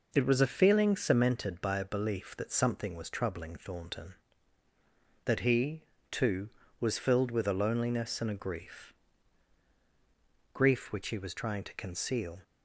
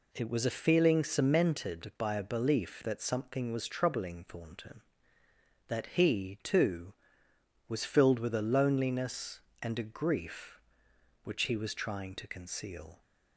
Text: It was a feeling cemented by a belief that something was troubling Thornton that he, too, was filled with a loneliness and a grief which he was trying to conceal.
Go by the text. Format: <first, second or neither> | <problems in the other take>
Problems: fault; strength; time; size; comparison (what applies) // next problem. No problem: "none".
second | says "grief" twice; at 10.5 s